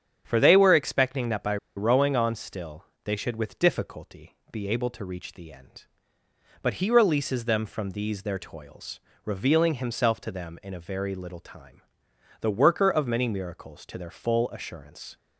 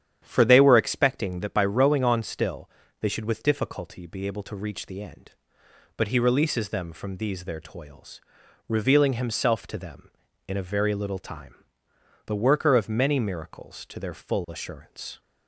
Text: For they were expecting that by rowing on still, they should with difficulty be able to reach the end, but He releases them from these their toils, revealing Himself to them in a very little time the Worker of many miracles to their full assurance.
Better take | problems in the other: second | starts louder than the rest; strong; until 1.2 s; 8.5 dB; strong in the second // pauses between "by" and "rowing"; slight; at 1.5 s; 0.20 s long // pauses between "difficulty" and "be"; slight; at 4.3 s; 0.16 s long // pauses between "time" and "the"; noticeable; at 11.7 s; 0.62 s long; noticeable in the second

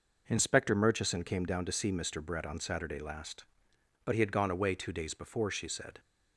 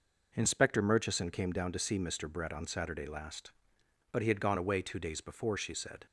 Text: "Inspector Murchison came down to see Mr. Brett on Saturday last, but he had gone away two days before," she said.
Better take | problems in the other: neither | none

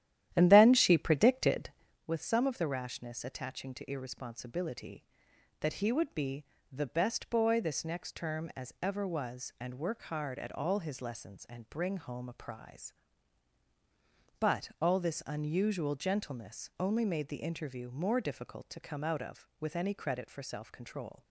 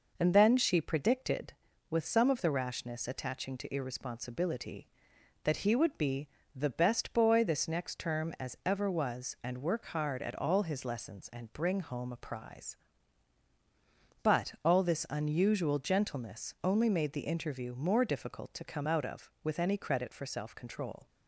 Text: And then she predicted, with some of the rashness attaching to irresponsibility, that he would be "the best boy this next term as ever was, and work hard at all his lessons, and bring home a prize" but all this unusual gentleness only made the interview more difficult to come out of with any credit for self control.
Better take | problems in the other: second | starts louder than the rest; strong; until 2.1 s; 11.5 dB // pauses between "be" and "the"; slight; at 6.4 s; 0.26 s long; slight in the second

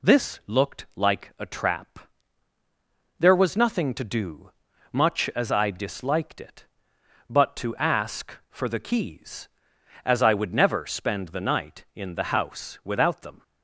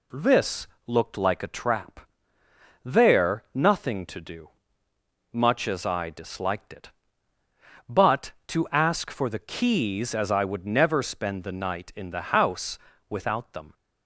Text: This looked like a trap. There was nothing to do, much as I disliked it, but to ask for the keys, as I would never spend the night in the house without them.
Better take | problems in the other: first | pauses between "This" and "looked"; slight; at 0.6 s; 0.20 s long // skips "was"; at 3.4 s // pauses between "house" and "without"; slight; at 12.7 s; 0.32 s long

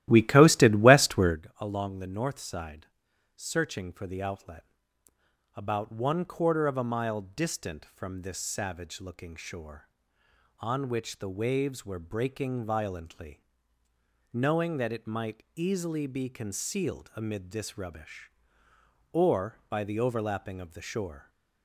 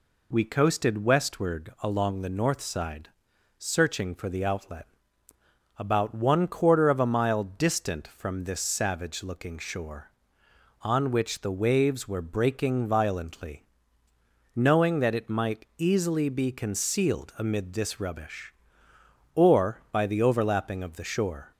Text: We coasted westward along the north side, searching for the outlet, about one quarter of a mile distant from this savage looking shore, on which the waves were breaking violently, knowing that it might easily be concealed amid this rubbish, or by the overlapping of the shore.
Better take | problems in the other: second | starts louder than the rest; strong; until 1.4 s; 14.5 dB

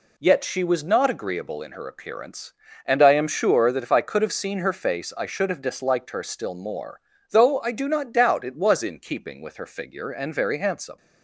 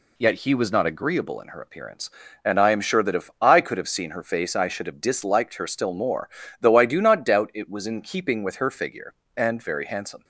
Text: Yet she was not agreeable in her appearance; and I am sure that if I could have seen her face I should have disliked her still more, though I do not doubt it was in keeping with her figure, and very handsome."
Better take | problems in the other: first | says "he" for "she"; at 0.3 s

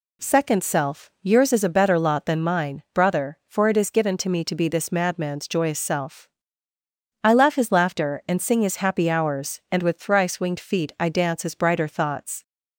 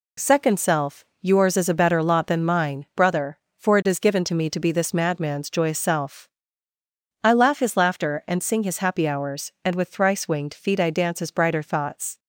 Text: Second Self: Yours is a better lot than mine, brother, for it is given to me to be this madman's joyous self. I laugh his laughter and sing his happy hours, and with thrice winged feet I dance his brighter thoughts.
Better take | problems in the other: neither | none

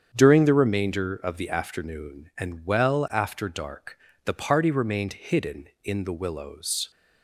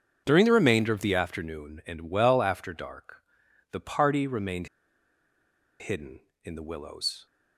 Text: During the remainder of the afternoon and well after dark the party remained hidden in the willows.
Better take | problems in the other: first | starts louder than the rest; strong; until 1.2 s; 7.5 dB; strong in the first // pauses between "dark" and "the"; noticeable; at 3.2 s; 0.50 s long; slight in the first // pauses between "remained" and "hidden"; at 4.6 s; 1.1 s long

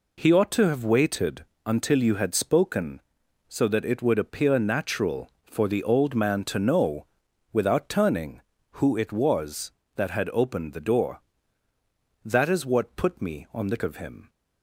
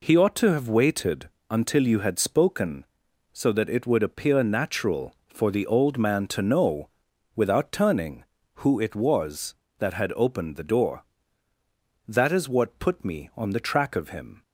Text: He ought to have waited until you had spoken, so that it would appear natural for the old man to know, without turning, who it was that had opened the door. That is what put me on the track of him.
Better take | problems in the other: second | pauses between "waited" and "until"; slight; at 1.4 s; 0.20 s long; slight in the second // skips "track"; at 13.7 s

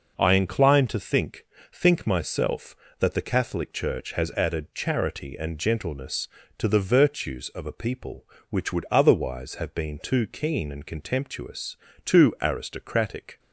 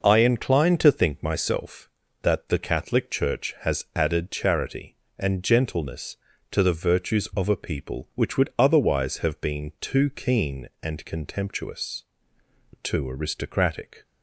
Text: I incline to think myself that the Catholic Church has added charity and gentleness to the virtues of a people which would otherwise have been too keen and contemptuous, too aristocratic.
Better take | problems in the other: second | says "think" twice; at 1.7 s

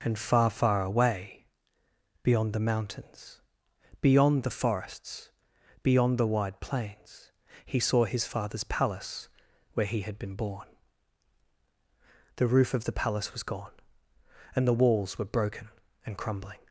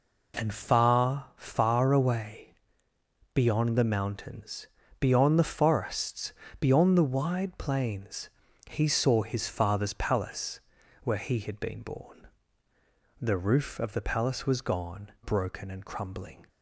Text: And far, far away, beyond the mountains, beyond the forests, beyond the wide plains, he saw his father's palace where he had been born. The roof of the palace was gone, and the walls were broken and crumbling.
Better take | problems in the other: first | pauses between "palace" and "where"; at 10.5 s; 0.44 s long; also in the first // skips "and the walls were"; at 15.1 s

